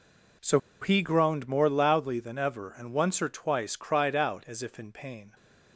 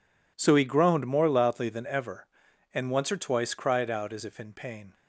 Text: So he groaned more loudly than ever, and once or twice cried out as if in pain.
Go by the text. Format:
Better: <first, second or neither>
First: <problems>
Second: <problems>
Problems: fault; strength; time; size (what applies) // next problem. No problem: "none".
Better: second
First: pauses between "So" and "he"; slight; at 0.5 s; 0.22 s long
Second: none